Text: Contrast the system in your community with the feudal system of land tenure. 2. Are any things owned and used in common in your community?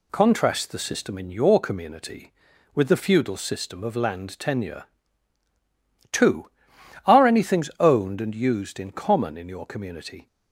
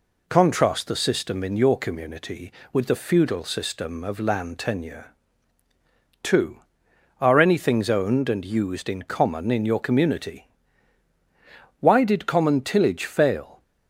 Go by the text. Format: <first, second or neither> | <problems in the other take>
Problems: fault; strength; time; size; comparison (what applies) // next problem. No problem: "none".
first | goes on to say "Why did common tillage fail"; strong; from 11.8 s on; 1.8 s long